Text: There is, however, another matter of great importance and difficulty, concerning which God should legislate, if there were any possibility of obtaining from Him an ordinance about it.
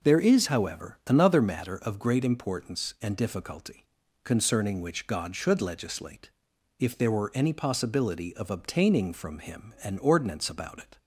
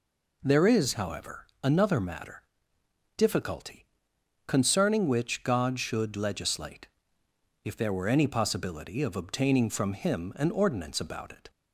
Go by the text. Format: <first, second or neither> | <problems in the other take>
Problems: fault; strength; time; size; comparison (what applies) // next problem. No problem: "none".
first | skips "of great importance and"; at 2.7 s